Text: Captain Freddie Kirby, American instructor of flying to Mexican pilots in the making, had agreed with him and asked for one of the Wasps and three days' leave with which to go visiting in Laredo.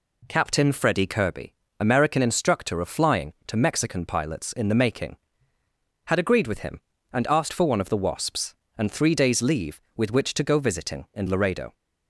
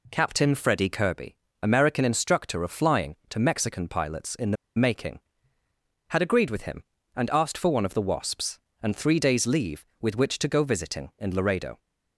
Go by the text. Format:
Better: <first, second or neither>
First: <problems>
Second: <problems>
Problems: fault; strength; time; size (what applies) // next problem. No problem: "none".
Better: first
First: none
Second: pauses between "the" and "making"; slight; at 4.5 s; 0.22 s long